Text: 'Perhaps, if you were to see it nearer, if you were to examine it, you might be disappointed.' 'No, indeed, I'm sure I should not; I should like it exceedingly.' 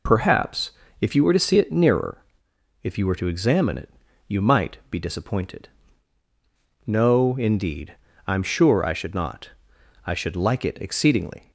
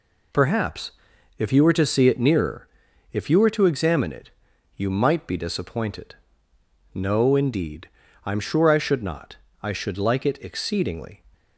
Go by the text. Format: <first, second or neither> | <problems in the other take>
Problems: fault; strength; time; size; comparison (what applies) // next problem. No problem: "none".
neither | none